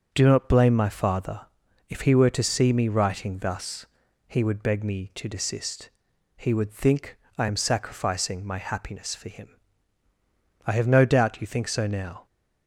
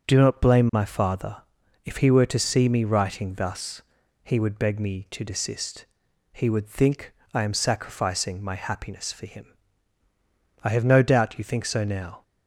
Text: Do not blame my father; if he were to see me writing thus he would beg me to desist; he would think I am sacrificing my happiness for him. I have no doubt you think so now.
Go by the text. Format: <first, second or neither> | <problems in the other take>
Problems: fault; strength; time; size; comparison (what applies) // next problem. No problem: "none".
neither | starts louder than the rest; the same in both // pauses between "thus" and "he"; the same in both // pauses between "think" and "I"; slight; the same in both